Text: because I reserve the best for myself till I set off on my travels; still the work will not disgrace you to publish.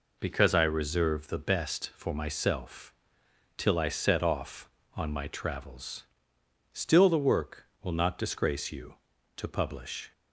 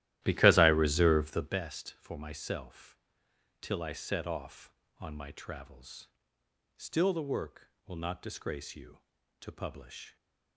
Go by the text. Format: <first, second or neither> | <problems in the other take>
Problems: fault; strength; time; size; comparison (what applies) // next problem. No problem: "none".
first | starts louder than the rest; strong; until 1.6 s; 14.5 dB // pauses between "myself" and "till"; noticeable; at 2.9 s; 0.64 s long; noticeable in the first